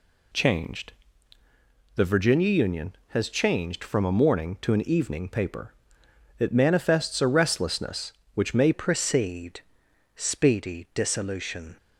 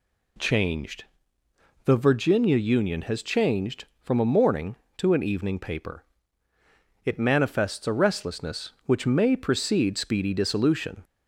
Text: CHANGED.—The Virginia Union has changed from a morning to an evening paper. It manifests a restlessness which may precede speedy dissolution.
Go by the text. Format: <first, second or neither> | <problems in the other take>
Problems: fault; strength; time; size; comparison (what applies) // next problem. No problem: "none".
second | changes voice at "precede"; from 8.7 s on; 3.0 s long // pauses between "precede" and "speedy"; noticeable; at 9.6 s; 0.56 s long